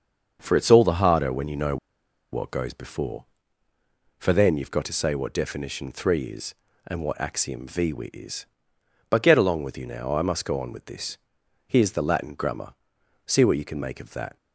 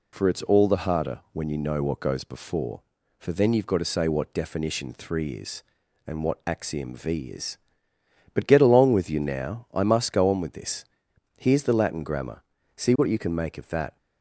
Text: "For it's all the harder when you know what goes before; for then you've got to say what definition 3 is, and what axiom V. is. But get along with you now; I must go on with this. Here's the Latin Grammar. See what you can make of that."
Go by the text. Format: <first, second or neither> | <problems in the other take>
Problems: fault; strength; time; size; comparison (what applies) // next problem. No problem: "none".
second | starts louder than the rest; until 1.4 s; 6.5 dB // pauses between "know" and "what"; noticeable; at 1.7 s; 0.55 s long